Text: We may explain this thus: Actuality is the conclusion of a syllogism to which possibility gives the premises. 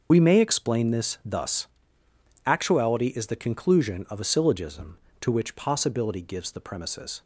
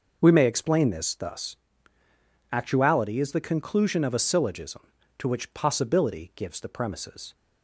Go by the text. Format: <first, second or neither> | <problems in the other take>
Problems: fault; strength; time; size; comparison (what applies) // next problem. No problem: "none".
second | loses the start of "We"; at 0.1 s; 60 ms // starts louder than the rest; until 1.1 s; 6.5 dB